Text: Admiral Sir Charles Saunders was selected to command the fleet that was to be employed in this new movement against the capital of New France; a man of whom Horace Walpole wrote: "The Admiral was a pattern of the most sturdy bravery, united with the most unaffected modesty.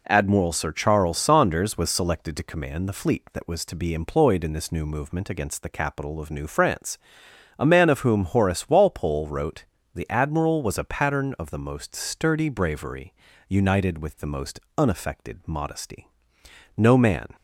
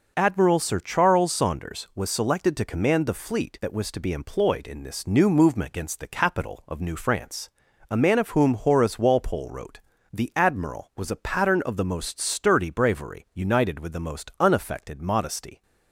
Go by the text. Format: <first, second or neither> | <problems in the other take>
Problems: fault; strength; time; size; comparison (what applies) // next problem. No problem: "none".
second | pauses between "most" and "unaffected"; slight; at 14.5 s; 0.20 s long // goes on to say "No man"; from 16.7 s on; 0.52 s long